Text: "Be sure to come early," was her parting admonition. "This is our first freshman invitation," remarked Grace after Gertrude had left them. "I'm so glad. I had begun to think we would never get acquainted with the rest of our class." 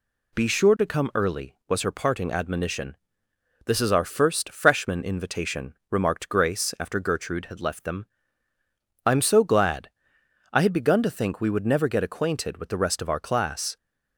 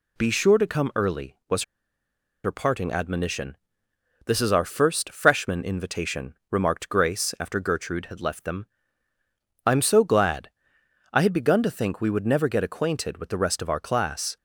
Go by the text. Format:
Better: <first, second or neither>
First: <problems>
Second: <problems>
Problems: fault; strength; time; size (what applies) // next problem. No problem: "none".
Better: first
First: none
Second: pauses between "was" and "her"; noticeable; at 1.6 s; 0.81 s long